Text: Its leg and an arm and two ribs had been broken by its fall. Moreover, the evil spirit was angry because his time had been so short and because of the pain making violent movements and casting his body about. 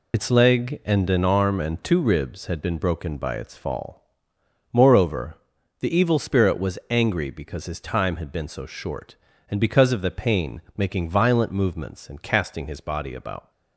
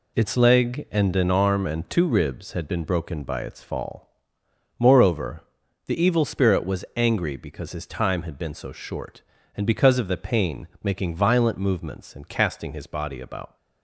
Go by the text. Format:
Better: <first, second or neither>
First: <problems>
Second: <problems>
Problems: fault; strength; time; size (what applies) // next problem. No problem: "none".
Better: second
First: loses the start of "Its"; at 0.1 s; 45 ms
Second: none